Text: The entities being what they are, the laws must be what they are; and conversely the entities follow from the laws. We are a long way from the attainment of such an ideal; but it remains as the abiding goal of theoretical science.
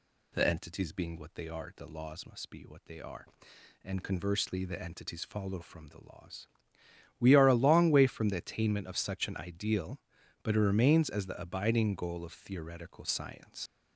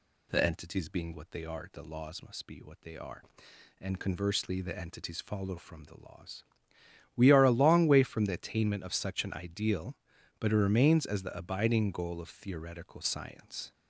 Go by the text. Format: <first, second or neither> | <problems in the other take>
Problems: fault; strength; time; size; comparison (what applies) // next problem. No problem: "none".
second | leaves "science" unfinished; at 13.6 s; 95 ms